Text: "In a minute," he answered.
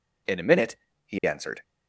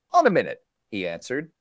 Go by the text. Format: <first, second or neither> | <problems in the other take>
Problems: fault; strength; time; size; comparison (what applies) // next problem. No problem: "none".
first | says "On" for "In"; at 0.1 s